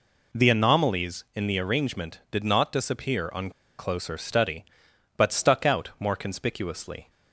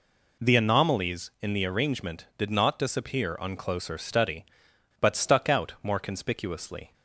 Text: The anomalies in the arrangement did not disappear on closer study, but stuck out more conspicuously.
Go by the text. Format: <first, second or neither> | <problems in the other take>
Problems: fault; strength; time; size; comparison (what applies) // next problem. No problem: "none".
second | pauses between "on" and "closer"; slight; at 3.4 s; 0.29 s long